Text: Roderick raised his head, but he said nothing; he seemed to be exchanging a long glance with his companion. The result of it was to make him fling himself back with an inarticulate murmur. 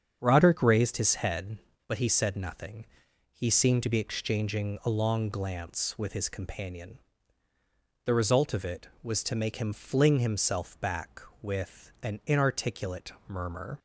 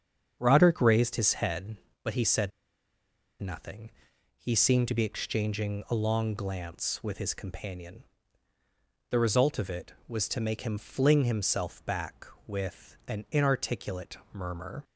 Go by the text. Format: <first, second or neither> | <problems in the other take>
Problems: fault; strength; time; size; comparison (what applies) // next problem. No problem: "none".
first | starts louder than the rest; strong; until 1.4 s; 7.5 dB; strong in the first // pauses between "said" and "nothing"; noticeable; at 2.5 s; 0.89 s long // pauses between "inarticulate" and "murmur"; slight; at 14.1 s; 0.16 s long; slight in the first